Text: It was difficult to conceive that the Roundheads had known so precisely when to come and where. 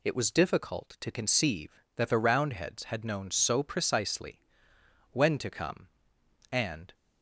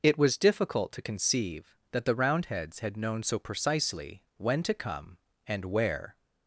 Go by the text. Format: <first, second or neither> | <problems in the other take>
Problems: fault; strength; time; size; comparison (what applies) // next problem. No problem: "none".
second | pauses between "precisely" and "when"; noticeable; at 4.3 s; 0.72 s long // stops before "where"; at 6.9 s